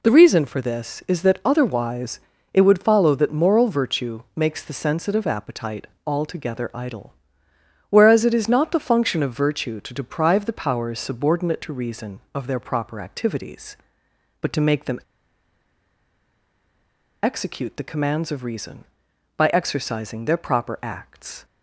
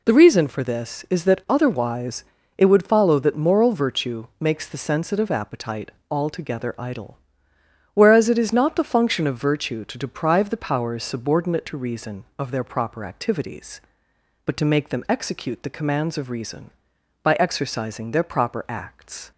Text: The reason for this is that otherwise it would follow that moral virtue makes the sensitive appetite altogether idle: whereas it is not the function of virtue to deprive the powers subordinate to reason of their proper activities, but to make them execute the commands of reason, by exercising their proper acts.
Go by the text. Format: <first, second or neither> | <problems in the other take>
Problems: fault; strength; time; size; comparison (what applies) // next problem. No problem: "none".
second | pauses between "otherwise" and "it"; slight; at 2.2 s; 0.32 s long; slight in the second // pauses between "appetite" and "altogether"; slight; at 5.8 s; 0.18 s long; slight in the second // pauses between "them" and "execute"; strong; at 15.0 s; 2.2 s long